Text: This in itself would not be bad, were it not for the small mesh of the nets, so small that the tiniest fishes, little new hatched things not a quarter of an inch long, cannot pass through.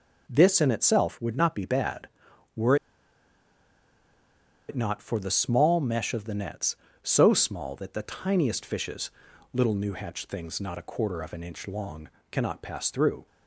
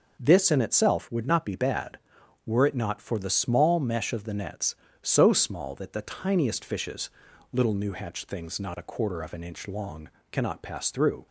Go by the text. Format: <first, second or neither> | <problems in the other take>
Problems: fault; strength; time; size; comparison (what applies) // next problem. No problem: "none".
second | pauses between "were" and "it"; strong; at 2.7 s; 1.9 s long